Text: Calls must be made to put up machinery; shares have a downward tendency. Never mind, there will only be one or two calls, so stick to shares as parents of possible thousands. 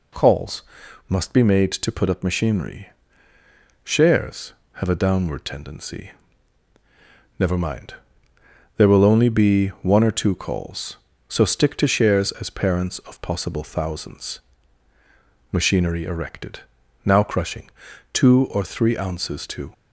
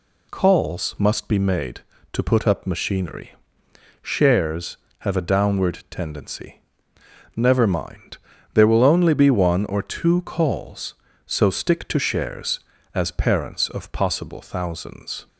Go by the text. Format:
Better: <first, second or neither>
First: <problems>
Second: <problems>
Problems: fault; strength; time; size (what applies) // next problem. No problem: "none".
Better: second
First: pauses between "Calls" and "must"; noticeable; at 0.6 s; 0.46 s long // goes on to say "Machinery erected now crushing two or three ounces to"; strong; from 15.5 s on; 4.2 s long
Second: none